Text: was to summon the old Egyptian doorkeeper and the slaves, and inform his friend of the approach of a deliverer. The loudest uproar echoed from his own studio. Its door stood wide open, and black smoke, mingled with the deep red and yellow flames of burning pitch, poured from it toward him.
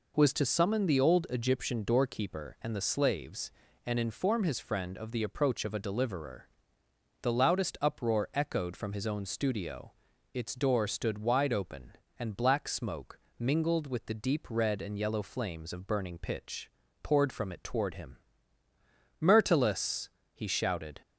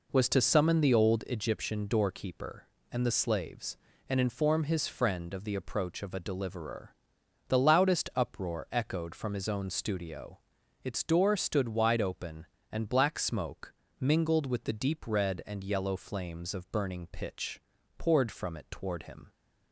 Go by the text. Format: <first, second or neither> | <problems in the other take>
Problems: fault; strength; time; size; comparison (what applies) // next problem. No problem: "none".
second | goes on to say "Myrtilus he shouted"; strong; from 19.1 s on; 1.8 s long